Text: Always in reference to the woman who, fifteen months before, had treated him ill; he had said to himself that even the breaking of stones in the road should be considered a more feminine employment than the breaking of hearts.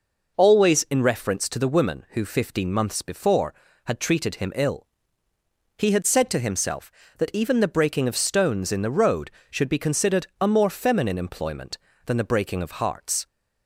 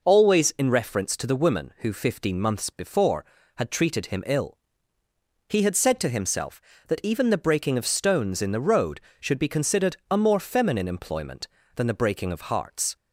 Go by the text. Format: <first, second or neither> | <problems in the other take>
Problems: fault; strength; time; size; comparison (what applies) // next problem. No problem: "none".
neither | none